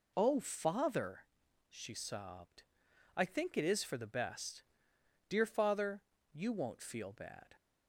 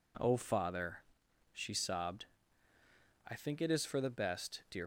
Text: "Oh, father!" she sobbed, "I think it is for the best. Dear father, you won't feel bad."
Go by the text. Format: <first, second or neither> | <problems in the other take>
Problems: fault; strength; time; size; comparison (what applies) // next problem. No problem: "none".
first | stops before "father you won't feel bad"; at 4.8 s